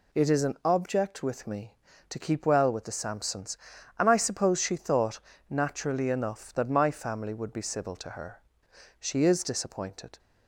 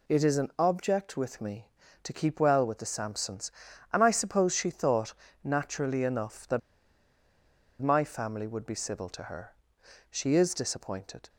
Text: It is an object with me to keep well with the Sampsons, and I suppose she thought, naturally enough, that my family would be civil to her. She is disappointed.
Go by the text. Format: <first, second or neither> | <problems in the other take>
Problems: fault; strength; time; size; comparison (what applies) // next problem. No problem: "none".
first | pauses between "that" and "my"; at 6.6 s; 1.2 s long